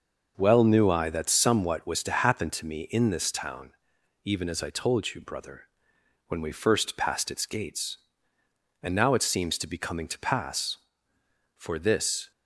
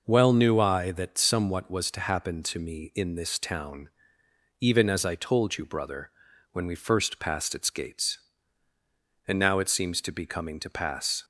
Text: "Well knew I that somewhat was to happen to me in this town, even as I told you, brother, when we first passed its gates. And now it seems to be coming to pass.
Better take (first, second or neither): second